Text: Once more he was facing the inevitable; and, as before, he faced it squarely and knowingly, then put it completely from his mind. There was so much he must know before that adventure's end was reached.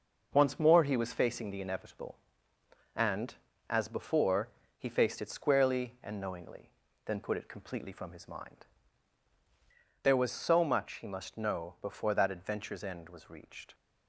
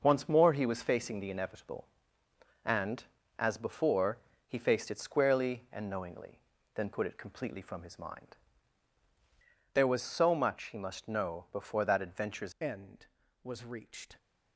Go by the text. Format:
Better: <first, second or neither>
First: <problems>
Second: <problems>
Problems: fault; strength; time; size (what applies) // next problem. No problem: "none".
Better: first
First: none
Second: changes voice at "end"; from 12.5 s on; 1.6 s long